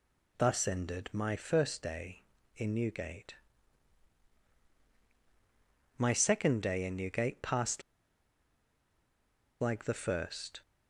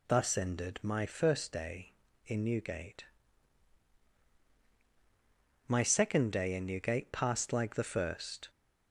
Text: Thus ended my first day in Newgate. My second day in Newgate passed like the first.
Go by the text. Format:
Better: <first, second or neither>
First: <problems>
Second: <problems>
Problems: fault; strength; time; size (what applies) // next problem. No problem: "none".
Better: second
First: pauses between "passed" and "like"; strong; at 7.8 s; 1.7 s long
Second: none